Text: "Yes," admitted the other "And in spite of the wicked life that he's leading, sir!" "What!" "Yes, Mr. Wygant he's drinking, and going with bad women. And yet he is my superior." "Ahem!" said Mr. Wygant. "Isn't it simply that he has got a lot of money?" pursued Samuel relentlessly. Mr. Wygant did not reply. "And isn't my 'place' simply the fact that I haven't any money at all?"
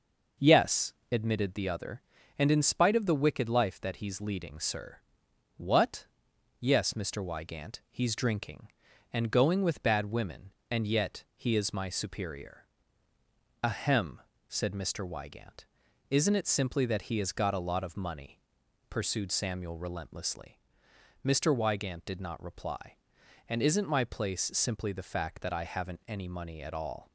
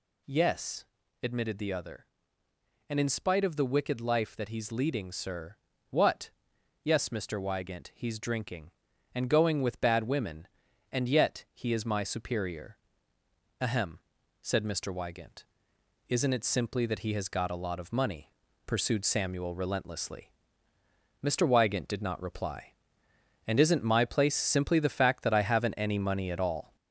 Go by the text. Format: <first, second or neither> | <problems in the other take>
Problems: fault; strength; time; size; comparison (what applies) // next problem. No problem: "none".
first | gets louder; noticeable; throughout; 4 dB